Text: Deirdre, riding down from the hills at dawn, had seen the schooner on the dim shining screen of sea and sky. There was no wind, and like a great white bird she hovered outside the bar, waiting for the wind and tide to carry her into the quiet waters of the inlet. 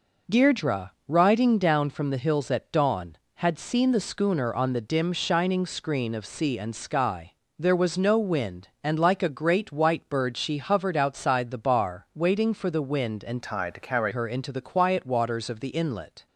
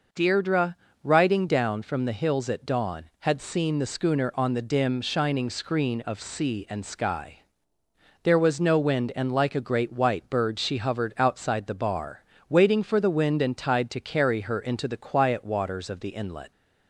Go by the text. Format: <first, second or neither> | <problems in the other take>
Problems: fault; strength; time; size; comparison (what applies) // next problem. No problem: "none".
second | changes voice from "tide" to "carry"; from 13.4 to 14.1 s; 0.7 s long